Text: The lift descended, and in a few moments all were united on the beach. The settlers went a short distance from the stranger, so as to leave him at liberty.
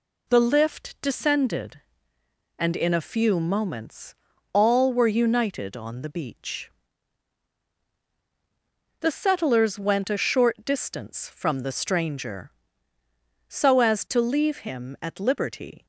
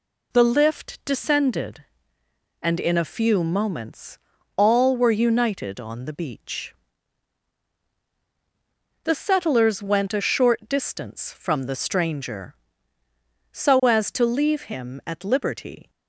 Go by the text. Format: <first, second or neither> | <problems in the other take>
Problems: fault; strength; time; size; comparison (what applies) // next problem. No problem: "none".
neither | pauses between "moments" and "all"; the same in both